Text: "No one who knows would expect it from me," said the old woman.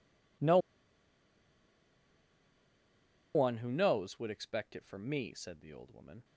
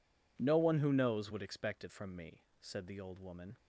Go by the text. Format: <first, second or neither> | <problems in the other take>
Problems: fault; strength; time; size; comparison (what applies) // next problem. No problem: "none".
second | pauses between "No" and "one"; strong; at 0.5 s; 2.7 s long